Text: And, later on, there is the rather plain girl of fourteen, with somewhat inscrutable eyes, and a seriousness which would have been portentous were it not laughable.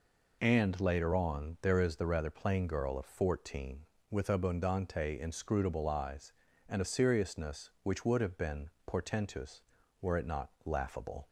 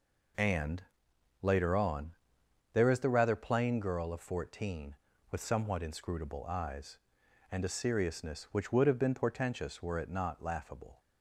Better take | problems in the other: second | says "abundante" for "somewhat"; at 4.2 s // pauses between "been" and "portentous"; slight; at 8.6 s; 0.18 s long // pauses between "not" and "laughable"; slight; at 10.4 s; 0.16 s long

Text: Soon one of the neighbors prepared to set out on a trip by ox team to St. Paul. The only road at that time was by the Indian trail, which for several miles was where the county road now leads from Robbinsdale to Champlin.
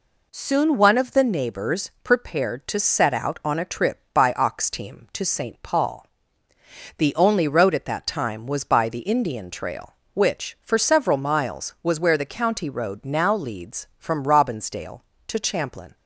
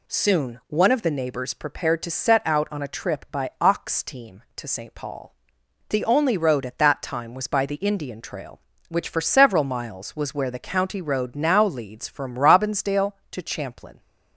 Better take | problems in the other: neither | none

